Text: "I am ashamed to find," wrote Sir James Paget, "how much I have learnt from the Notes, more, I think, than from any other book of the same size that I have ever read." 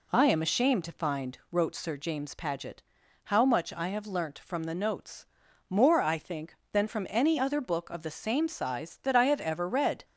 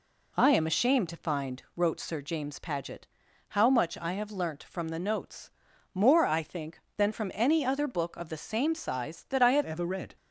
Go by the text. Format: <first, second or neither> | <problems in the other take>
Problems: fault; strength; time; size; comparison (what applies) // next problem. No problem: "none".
first | changes voice at "ever"; from 9.6 s on; 0.5 s long